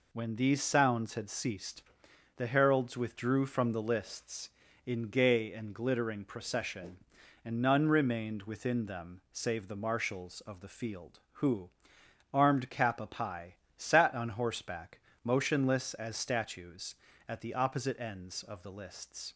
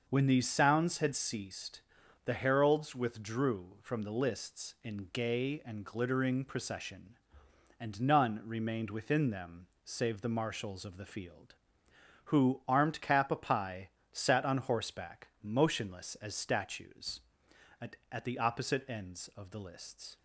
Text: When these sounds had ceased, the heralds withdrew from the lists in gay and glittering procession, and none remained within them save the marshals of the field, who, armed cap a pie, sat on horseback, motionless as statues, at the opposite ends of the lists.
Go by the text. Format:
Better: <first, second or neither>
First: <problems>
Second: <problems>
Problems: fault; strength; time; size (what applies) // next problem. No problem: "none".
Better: first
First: none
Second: starts louder than the rest; until 1.0 s; 6 dB // pauses between "them" and "save"; slight; at 9.6 s; 0.16 s long // says "at" twice; at 18.0 s